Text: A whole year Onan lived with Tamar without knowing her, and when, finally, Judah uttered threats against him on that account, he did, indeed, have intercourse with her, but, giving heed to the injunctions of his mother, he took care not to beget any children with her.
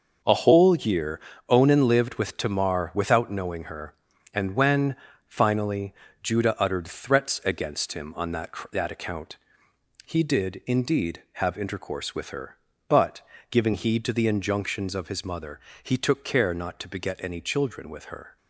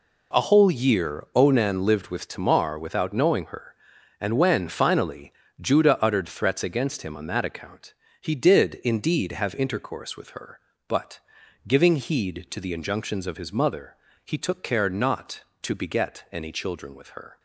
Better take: second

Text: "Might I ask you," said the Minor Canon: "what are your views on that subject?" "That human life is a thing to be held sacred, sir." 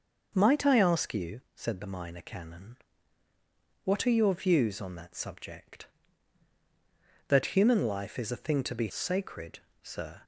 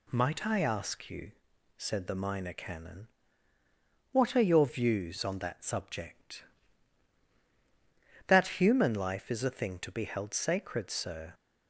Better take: second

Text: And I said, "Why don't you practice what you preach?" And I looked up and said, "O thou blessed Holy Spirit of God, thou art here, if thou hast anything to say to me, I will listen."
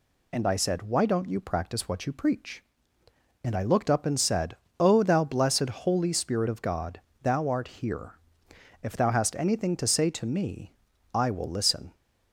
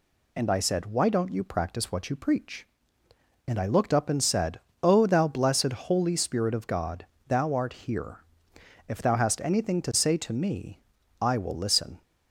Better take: neither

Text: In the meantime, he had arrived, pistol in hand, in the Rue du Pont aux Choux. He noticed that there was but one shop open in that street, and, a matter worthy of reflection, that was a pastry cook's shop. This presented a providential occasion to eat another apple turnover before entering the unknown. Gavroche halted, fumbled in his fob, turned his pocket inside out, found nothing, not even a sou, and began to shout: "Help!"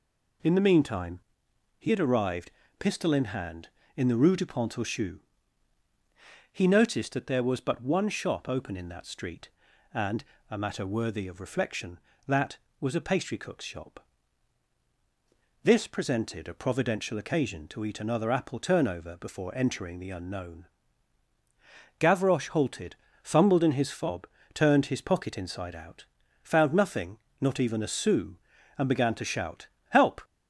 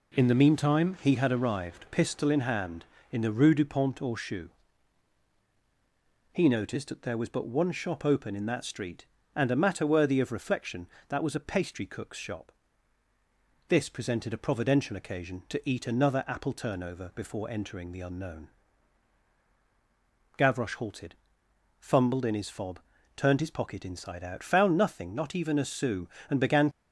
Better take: first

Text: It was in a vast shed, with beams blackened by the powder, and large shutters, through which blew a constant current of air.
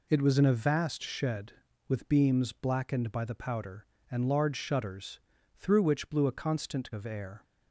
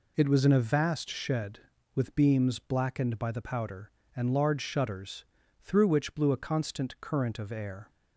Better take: second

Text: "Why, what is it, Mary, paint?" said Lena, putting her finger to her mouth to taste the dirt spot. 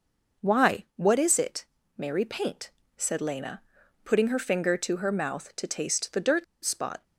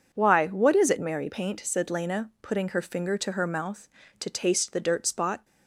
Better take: second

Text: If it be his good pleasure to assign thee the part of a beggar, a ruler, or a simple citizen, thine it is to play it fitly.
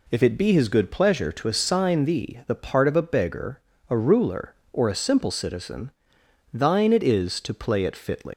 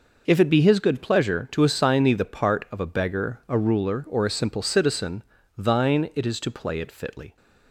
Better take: second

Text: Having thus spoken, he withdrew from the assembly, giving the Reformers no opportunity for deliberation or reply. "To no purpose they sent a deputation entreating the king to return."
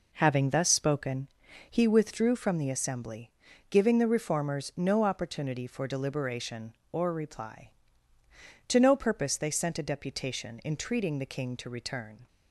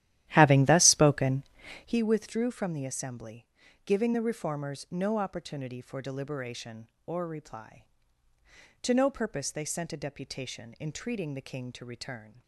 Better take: first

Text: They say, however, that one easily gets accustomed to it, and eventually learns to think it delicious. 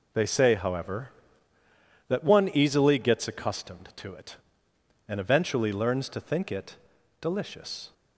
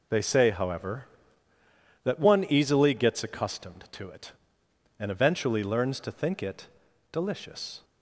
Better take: neither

